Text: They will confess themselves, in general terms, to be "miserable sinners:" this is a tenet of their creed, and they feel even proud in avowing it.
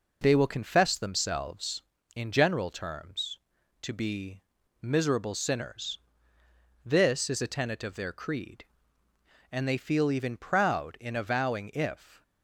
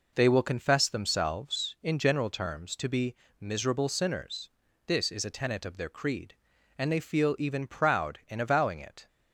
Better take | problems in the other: second | pauses between "be" and "miserable"; at 4.4 s; 0.40 s long; slight in the second // says "if" for "it"; at 11.7 s

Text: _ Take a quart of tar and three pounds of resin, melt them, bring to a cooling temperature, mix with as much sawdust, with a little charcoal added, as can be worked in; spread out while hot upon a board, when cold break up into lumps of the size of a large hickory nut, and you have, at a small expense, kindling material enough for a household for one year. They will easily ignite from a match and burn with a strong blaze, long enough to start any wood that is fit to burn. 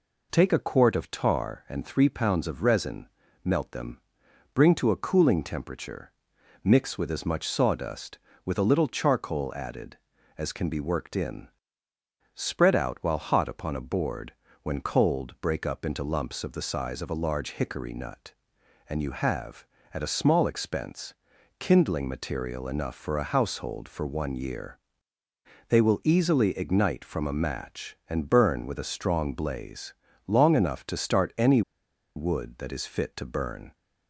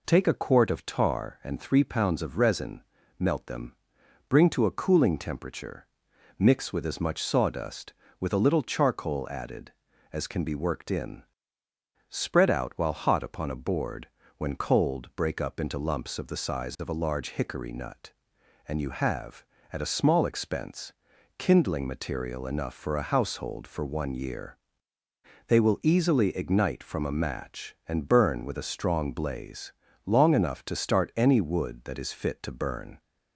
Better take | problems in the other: second | pauses between "any" and "wood"; noticeable; at 31.6 s; 0.55 s long

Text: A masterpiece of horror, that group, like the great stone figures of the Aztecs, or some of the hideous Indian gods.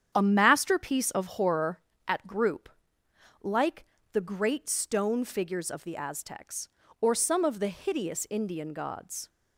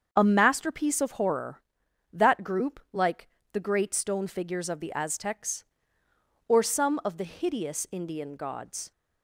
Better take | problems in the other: second | starts louder than the rest; strong; until 1.1 s; 9 dB; also in the second // says "at" for "that"; at 2.0 s // pauses between "like" and "the"; slight; at 3.8 s; 0.28 s long; slight in the second

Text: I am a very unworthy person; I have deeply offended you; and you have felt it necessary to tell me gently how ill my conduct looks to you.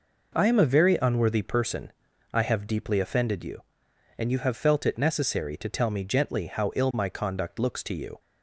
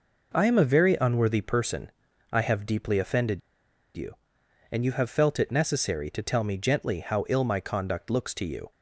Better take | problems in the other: first | pauses between "offended" and "you"; noticeable; at 3.4 s; 0.56 s long

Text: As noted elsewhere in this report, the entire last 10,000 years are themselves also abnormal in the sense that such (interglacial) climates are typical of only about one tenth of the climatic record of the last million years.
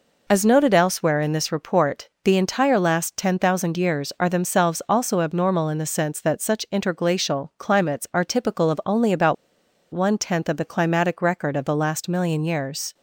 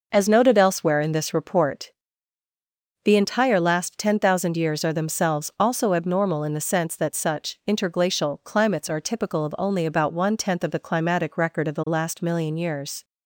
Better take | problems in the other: second | pauses between "about" and "one"; noticeable; at 9.3 s; 0.58 s long

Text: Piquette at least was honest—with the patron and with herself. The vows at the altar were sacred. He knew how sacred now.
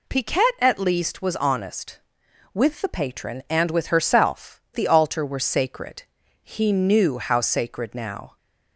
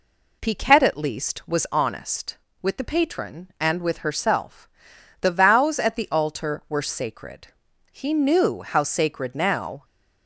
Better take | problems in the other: second | skips "The vows at"; at 4.6 s

